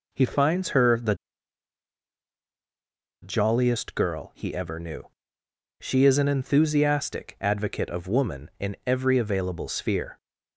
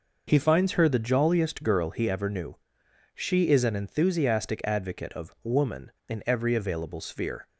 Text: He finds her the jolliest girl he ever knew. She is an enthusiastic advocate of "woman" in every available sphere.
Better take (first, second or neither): second